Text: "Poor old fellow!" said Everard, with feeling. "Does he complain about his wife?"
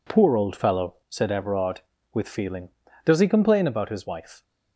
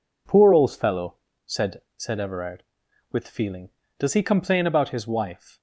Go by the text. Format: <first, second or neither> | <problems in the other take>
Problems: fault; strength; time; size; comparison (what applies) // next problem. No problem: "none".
first | says "said" twice; at 1.9 s